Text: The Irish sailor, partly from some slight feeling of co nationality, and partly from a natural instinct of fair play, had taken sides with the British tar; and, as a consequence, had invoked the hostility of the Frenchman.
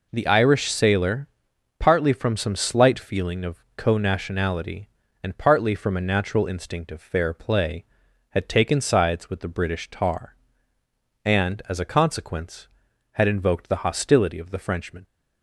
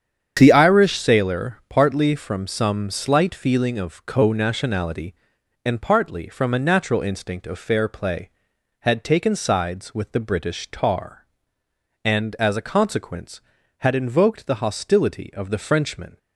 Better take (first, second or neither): first